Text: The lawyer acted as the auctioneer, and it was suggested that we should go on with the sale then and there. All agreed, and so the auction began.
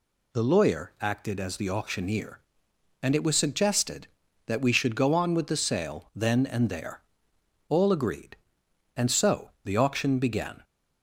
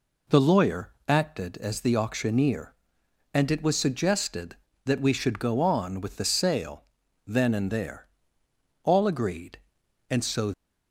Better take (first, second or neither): first